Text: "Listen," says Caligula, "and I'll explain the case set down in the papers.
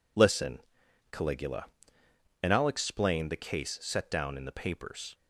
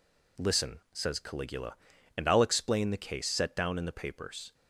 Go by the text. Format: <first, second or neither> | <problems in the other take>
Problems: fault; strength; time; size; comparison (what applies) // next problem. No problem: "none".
second | skips "says"; at 0.8 s